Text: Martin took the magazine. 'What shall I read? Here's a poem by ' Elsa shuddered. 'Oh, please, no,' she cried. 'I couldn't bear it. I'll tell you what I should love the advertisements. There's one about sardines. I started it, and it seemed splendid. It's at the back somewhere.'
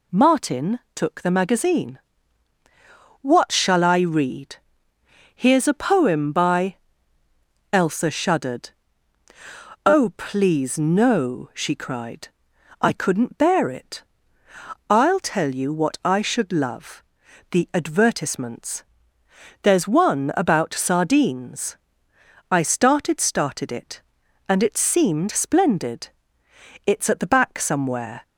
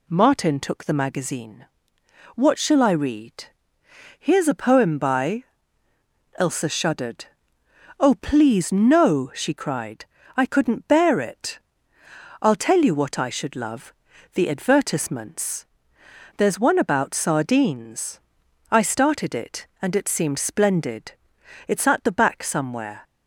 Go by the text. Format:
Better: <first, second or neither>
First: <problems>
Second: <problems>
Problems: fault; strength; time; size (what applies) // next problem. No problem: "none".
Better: second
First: pauses between "Martin" and "took"; slight; at 0.7 s; 0.16 s long // pauses between "love" and "the"; noticeable; at 17.0 s; 0.48 s long // says "started" twice; at 23.1 s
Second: pauses between "love" and "the"; at 13.9 s; 0.42 s long